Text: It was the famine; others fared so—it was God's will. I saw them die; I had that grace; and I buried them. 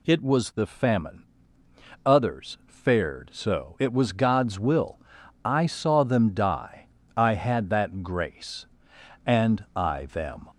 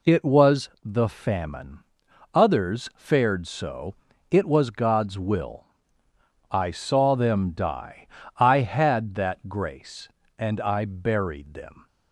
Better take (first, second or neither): second